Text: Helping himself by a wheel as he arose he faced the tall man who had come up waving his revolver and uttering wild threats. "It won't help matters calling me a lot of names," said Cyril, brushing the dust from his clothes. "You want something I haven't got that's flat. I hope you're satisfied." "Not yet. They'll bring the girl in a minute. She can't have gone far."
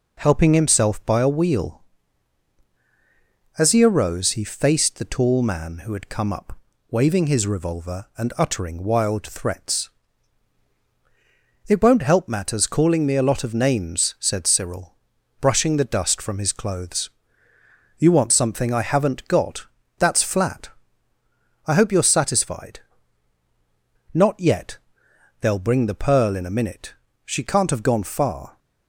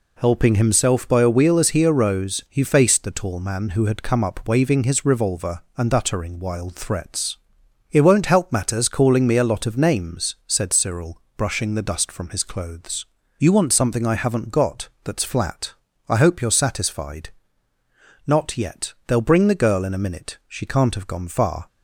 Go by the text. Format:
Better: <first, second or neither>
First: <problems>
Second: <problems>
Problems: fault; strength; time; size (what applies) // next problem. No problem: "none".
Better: second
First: pauses between "up" and "waving"; slight; at 6.5 s; 0.32 s long // pauses between "got" and "that's"; slight; at 19.6 s; 0.32 s long // says "pearl" for "girl"; at 26.0 s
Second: pauses between "got" and "that's"; slight; at 14.8 s; 0.16 s long